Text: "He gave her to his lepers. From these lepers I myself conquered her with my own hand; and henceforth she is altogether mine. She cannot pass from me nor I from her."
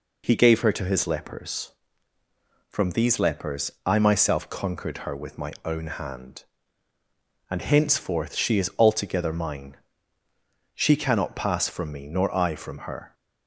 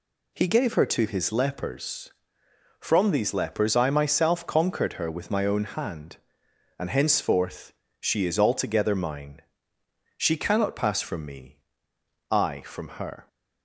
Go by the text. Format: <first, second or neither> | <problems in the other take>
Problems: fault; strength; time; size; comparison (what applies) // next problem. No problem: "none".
first | pauses between "henceforth" and "she"; slight; at 7.7 s; 0.28 s long // skips "nor"; at 11.9 s